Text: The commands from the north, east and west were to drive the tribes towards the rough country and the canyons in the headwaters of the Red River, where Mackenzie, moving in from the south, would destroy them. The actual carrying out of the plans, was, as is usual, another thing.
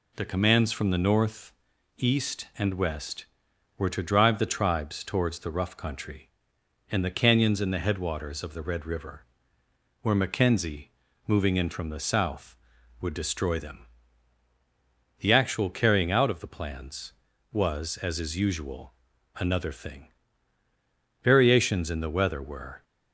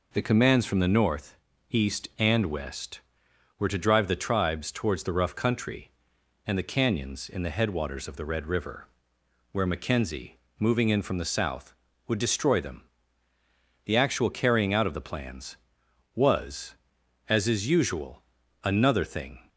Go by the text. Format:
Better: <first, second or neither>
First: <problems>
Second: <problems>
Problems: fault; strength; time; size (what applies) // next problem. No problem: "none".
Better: second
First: goes on to say "Variations in the weather were"; from 21.2 s on; 1.6 s long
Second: none